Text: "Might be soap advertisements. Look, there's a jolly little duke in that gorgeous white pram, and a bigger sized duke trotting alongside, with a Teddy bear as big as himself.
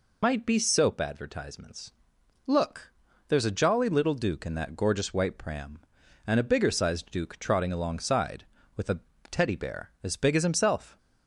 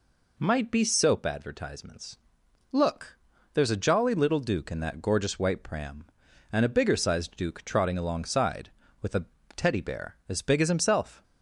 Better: second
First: loses the start of "Might"; at 0.2 s; 95 ms // pauses between "a" and "Teddy"; slight; at 9.0 s; 0.28 s long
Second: pauses between "a" and "Teddy"; slight; at 9.2 s; 0.28 s long

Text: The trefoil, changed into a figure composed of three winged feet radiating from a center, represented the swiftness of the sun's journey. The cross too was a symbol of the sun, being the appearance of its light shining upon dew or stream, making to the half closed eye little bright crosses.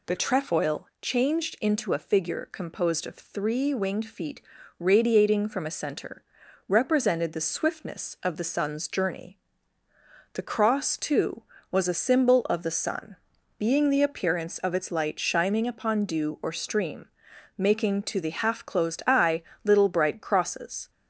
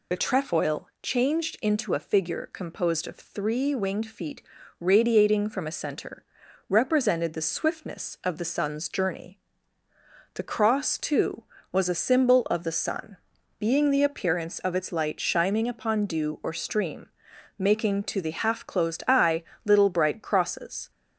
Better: first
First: pauses between "feet" and "radiating"; at 4.3 s; 0.40 s long // pauses between "eye" and "little"; slight; at 19.4 s; 0.22 s long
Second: loses the start of "The"; at 0.1 s; 30 ms // pauses between "feet" and "radiating"; at 4.3 s; 0.40 s long // pauses between "eye" and "little"; slight; at 19.4 s; 0.22 s long

